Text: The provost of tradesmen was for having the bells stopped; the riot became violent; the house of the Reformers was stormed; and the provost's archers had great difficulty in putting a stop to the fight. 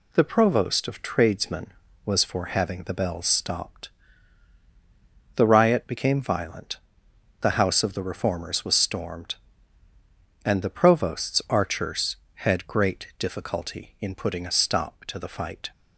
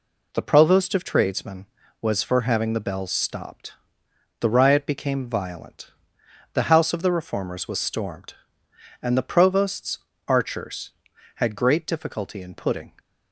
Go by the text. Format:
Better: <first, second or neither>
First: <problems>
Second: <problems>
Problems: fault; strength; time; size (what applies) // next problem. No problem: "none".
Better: first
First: none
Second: pauses between "provost's" and "archers"; slight; at 9.9 s; 0.32 s long // stops before "a stop to the fight"; at 12.9 s